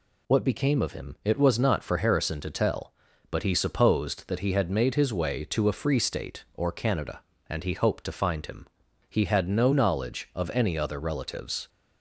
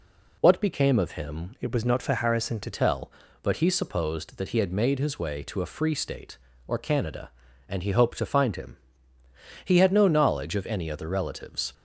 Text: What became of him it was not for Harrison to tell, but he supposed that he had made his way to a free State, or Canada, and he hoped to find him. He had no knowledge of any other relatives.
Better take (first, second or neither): first